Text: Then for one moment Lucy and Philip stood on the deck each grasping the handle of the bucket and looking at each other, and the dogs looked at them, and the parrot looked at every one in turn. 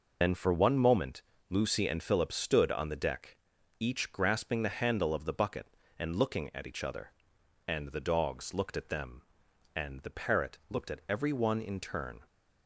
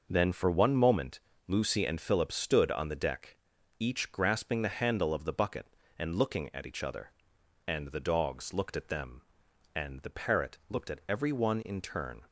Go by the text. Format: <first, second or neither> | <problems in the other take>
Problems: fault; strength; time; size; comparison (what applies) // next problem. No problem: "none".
second | loses the start of "Then"; at 0.2 s; 100 ms // pauses between "moment" and "Lucy"; slight; at 1.2 s; 0.28 s long; slight in the second // pauses between "deck" and "each"; at 3.3 s; 0.44 s long; also in the second